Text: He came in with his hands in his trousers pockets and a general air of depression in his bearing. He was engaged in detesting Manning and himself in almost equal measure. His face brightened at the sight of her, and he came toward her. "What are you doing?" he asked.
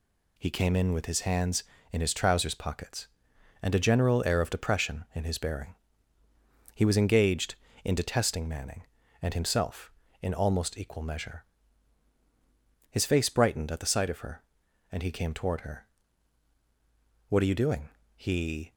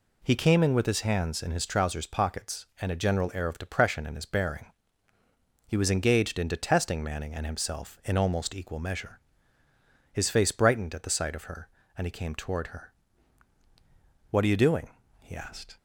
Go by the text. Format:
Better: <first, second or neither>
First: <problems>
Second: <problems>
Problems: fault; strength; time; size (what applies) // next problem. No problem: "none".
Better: second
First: stops before "asked"; at 18.7 s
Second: none